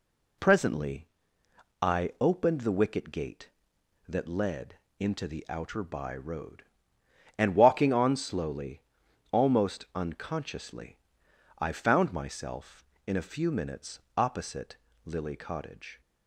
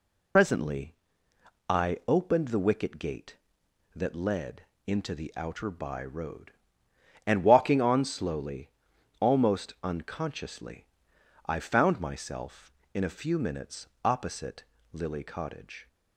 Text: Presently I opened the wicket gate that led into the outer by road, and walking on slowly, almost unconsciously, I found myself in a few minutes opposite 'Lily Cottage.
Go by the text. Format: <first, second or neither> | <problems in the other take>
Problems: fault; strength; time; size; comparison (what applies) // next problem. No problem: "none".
first | loses the start of "Presently"; at 0.3 s; 85 ms // pauses between "Presently" and "I"; noticeable; at 0.9 s; 0.76 s long; noticeable in the first // pauses between "led" and "into"; slight; at 4.6 s; 0.22 s long; slight in the first // pauses between "minutes" and "opposite"; slight; at 13.8 s; 0.18 s long; slight in the first // pauses between "opposite" and "Lily"; slight; at 14.6 s; 0.28 s long; slight in the first